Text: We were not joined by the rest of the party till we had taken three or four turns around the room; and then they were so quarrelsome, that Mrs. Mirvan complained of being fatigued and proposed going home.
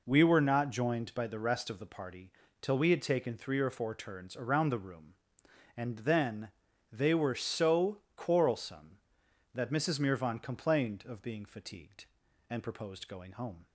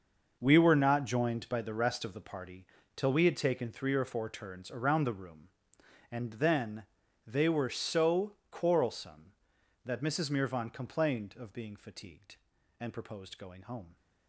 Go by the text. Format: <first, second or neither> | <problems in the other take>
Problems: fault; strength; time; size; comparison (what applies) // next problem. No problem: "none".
first | gets quieter; strong; throughout; 13 dB // pauses between "party" and "till"; slight; at 2.6 s; 0.28 s long; slight in the first // pauses between "then" and "they"; at 6.8 s; 0.42 s long; also in the first // pauses between "so" and "quarrelsome"; slight; at 8.3 s; 0.16 s long; slight in the first